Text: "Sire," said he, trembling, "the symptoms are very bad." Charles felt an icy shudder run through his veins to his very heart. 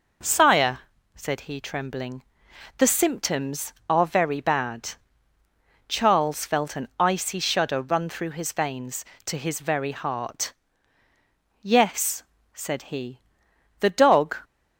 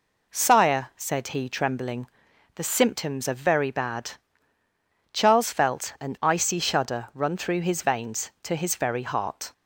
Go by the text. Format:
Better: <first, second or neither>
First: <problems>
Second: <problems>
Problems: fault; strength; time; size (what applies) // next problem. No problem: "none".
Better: second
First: goes on to say "Yes said he the dog"; strong; from 11.5 s on; 2.7 s long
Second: none